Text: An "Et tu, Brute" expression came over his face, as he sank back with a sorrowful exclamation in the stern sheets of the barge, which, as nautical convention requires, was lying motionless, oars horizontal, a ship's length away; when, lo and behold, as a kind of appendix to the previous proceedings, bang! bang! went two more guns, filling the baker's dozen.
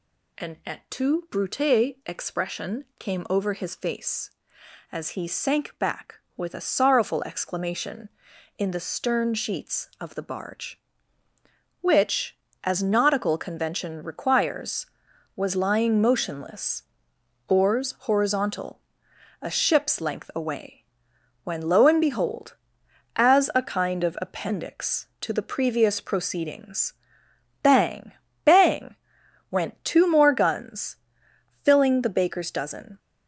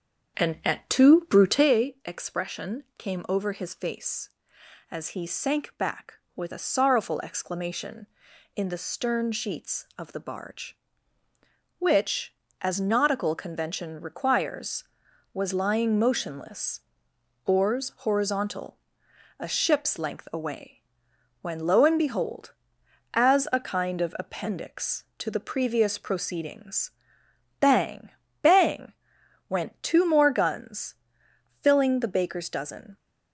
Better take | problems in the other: first | starts louder than the rest; strong; until 1.7 s; 7.5 dB

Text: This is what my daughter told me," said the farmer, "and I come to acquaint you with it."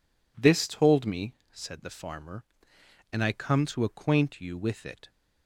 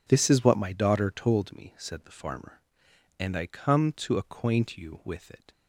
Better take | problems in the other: second | skips "is what my daughter"; at 0.6 s

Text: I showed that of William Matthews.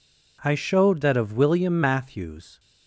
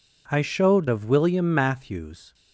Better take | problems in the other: first | skips "that"; at 0.8 s

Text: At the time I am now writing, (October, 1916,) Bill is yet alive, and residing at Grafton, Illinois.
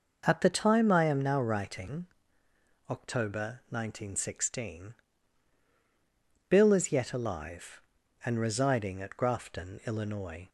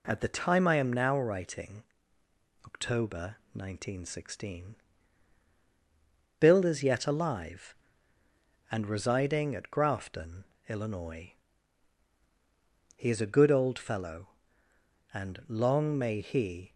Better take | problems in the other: first | goes on to say "He is a good old fellow and long may he"; strong; from 12.9 s on; 3.7 s long

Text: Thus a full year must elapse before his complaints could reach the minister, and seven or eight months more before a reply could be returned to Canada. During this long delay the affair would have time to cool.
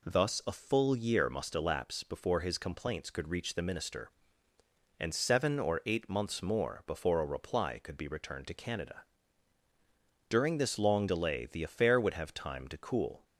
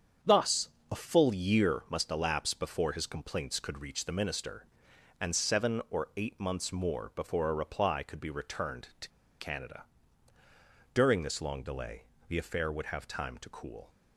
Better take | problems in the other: first | starts louder than the rest; strong; until 1.4 s; 7.5 dB // pauses between "Thus" and "a"; slight; at 0.6 s; 0.20 s long // pauses between "to" and "Canada"; slight; at 9.0 s; 0.31 s long // pauses between "delay" and "the"; slight; at 12.0 s; 0.26 s long

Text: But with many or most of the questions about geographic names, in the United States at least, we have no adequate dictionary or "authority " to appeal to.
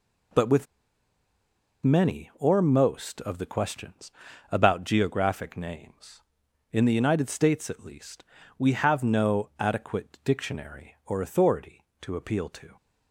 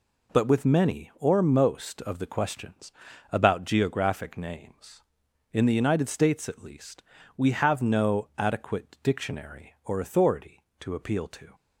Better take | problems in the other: second | pauses between "with" and "many"; at 0.6 s; 1.1 s long // pauses between "questions" and "about"; at 4.1 s; 0.40 s long; also in the second

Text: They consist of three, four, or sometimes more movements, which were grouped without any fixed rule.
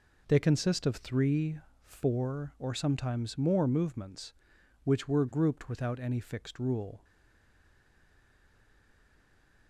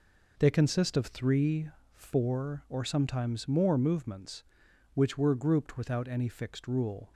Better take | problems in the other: second | stays silent after the last word; strong; from 7.0 s on; 2.6 s long

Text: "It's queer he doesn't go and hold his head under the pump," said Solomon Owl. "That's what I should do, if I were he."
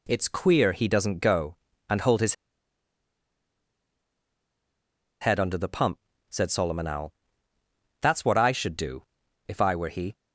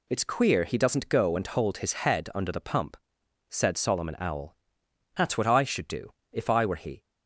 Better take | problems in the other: second | pauses between "his" and "head"; strong; at 2.3 s; 2.8 s long

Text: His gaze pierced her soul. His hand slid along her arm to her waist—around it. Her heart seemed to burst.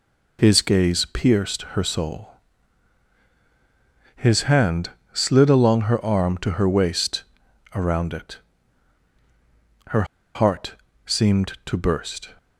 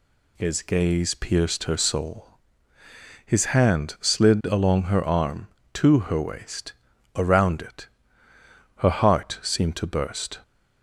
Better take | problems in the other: second | pauses between "hand" and "slid"; slight; at 4.8 s; 0.24 s long // pauses between "Her" and "heart"; slight; at 10.0 s; 0.31 s long // pauses between "heart" and "seemed"; slight; at 10.7 s; 0.32 s long

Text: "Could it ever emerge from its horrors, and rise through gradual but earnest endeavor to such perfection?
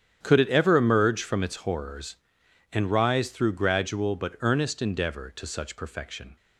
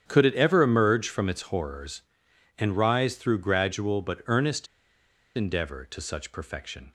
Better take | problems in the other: first | starts louder than the rest; strong; until 1.0 s; 9 dB; strong in the first // pauses between "earnest" and "endeavor"; noticeable; at 4.6 s; 0.71 s long

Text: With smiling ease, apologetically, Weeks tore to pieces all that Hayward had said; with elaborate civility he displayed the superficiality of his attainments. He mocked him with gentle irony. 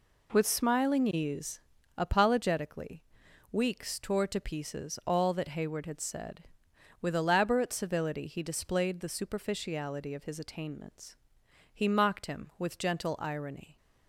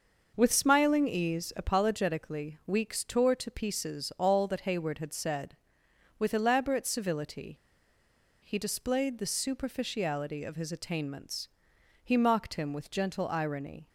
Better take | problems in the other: first | pauses between "civility" and "he"; noticeable; at 7.5 s; 0.87 s long

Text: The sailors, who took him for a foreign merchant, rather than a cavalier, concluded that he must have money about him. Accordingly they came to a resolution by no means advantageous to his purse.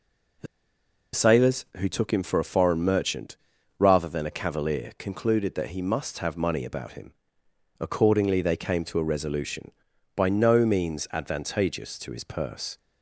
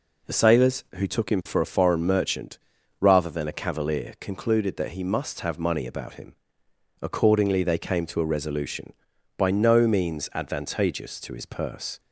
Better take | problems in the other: second | pauses between "The" and "sailors"; noticeable; at 0.4 s; 0.68 s long

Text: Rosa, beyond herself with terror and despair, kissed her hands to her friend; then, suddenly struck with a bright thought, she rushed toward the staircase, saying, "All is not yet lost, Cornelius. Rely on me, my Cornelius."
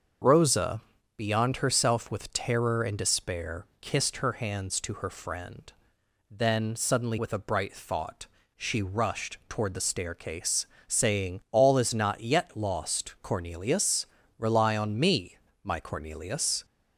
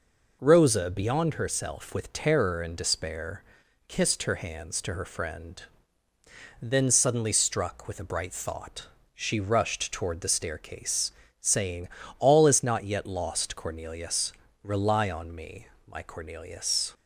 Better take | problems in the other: second | starts louder than the rest; until 1.5 s; 6.5 dB // skips "struck"; at 7.1 s

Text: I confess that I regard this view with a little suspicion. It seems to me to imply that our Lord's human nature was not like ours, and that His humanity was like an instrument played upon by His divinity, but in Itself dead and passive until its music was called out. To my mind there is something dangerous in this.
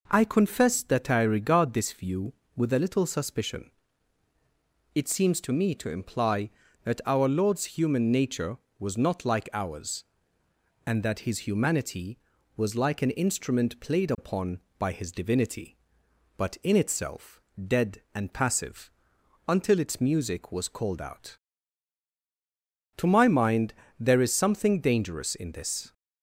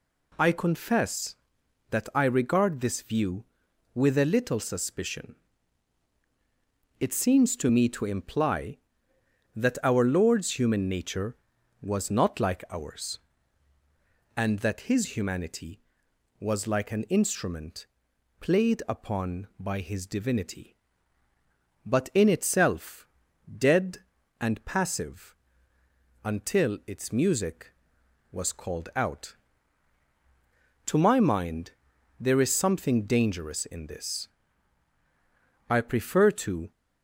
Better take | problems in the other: first | pauses between "instrument" and "played"; noticeable; at 17.8 s; 0.52 s long // pauses between "Itself" and "dead"; noticeable; at 23.0 s; 0.50 s long; slight in the first // pauses between "passive" and "until"; noticeable; at 25.3 s; 0.88 s long; noticeable in the first // pauses between "mind" and "there"; noticeable; at 31.7 s; 0.48 s long; slight in the first // goes on to say "I prefer to"; noticeable; from 35.6 s on; 1.0 s long

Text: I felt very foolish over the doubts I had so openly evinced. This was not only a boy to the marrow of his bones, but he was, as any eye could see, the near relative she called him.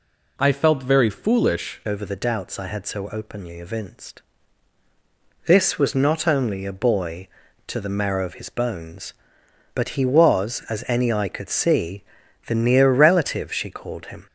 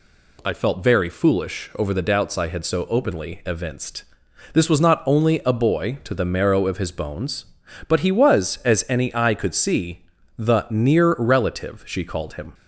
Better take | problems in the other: second | changes voice at "over"; from 1.8 s on; 12.4 s long

